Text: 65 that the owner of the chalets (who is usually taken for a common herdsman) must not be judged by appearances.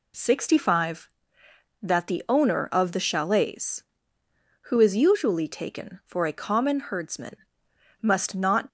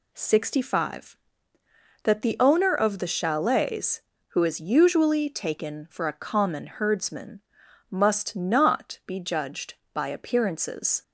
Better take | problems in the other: second | stops before "be judged by appearances"; at 8.6 s

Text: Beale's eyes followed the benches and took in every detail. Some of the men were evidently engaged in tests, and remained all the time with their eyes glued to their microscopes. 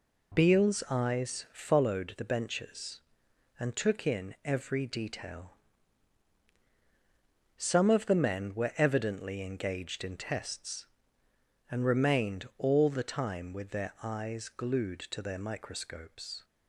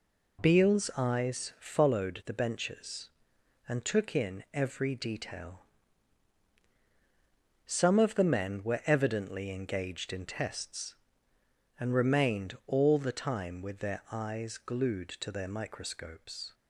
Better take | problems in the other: neither | none

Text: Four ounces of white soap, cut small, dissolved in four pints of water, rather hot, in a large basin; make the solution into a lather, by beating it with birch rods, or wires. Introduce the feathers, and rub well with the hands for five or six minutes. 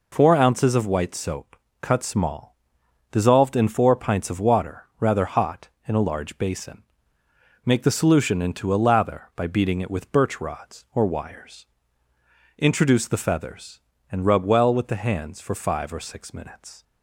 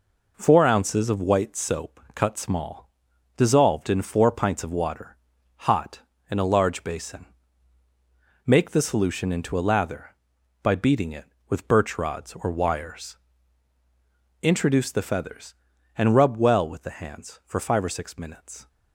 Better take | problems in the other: first | skips "rather"; at 5.3 s

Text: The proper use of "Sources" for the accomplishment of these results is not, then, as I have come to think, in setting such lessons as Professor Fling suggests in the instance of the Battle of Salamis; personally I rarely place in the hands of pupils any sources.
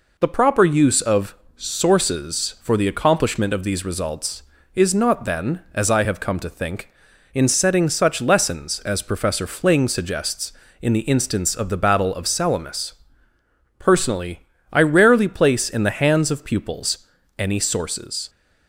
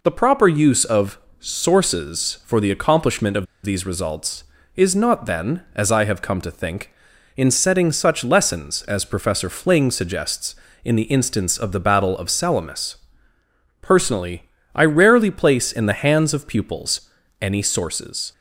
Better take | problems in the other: first | pauses between "of" and "Sources"; slight; at 1.1 s; 0.22 s long; slight in the first // pauses between "of" and "these"; slight; at 3.4 s; 0.18 s long // pauses between "personally" and "I"; slight; at 14.4 s; 0.32 s long; slight in the first // pauses between "pupils" and "any"; slight; at 17.1 s; 0.28 s long; slight in the first

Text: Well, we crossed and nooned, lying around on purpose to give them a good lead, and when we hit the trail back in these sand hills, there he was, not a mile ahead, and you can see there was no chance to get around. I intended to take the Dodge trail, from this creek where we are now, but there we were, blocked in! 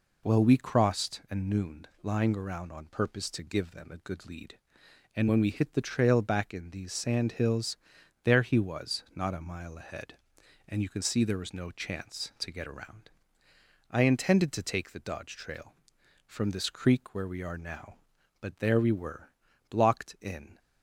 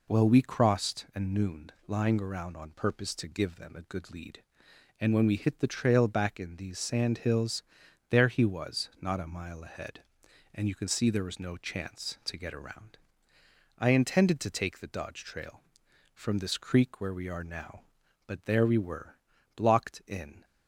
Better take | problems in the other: neither | none

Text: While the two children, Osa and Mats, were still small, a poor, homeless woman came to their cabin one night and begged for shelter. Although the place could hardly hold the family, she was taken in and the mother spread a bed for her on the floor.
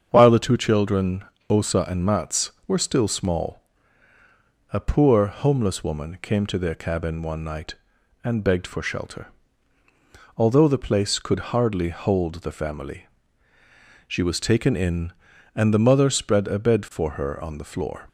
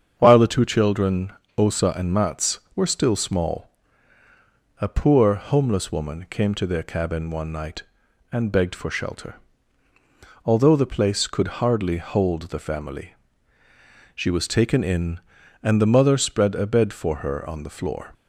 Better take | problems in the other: neither | starts louder than the rest; strong; the same in both

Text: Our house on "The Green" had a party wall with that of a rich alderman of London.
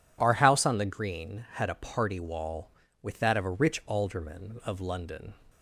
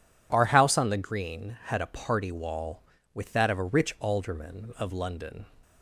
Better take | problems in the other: neither | none

